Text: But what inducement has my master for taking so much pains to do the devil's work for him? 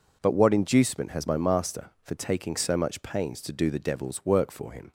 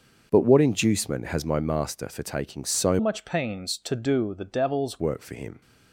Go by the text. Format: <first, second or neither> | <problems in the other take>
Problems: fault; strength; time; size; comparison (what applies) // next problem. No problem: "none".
first | starts louder than the rest; noticeable; until 1.3 s; 6 dB // changes voice from "much" to "devil's"; from 2.9 to 5.0 s; 2.1 s long